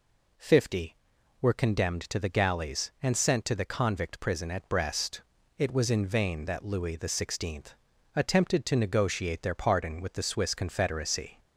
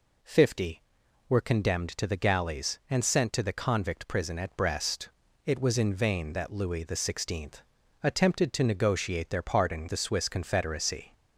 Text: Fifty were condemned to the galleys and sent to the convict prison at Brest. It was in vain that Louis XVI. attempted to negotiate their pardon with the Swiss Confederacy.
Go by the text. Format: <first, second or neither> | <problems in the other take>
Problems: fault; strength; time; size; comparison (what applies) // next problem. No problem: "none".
first | skips "with"; at 9.8 s